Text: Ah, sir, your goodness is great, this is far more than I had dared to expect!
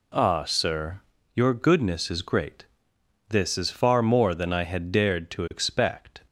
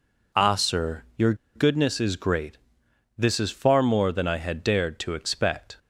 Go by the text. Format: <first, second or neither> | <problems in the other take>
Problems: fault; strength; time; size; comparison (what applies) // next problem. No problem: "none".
first | pauses between "your" and "goodness"; slight; at 1.3 s; 0.21 s long